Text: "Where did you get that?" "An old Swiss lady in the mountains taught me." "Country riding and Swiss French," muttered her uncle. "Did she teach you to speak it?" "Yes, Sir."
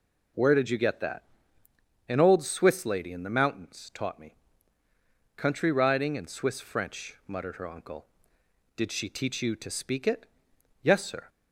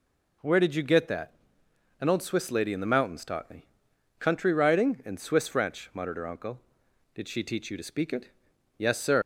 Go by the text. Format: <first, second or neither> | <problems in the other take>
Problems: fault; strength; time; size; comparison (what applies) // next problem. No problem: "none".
first | leaves "Sir" unfinished; at 9.2 s; 125 ms